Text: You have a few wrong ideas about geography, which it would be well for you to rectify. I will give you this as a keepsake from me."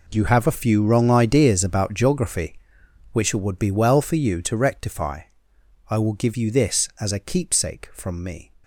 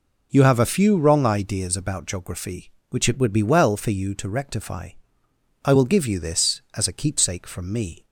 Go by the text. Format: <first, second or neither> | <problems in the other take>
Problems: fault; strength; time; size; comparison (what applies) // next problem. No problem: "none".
second | gets quieter; strong; throughout; 14 dB